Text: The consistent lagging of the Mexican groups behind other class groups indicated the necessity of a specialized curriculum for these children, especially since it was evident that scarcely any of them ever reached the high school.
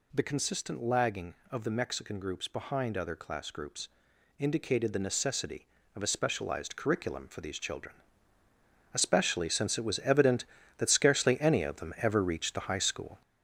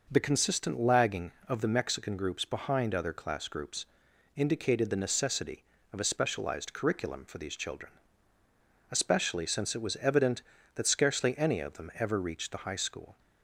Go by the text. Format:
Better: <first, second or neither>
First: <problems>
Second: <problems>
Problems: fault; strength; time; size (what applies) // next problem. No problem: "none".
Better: second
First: gets louder; noticeable; throughout; 5.5 dB // pauses between "groups" and "indicated"; noticeable; at 3.8 s; 0.52 s long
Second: pauses between "groups" and "indicated"; noticeable; at 3.8 s; 0.52 s long